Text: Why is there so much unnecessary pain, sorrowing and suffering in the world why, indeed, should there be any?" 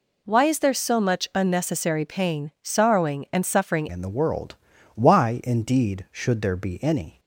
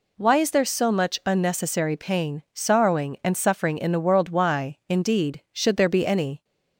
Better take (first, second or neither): second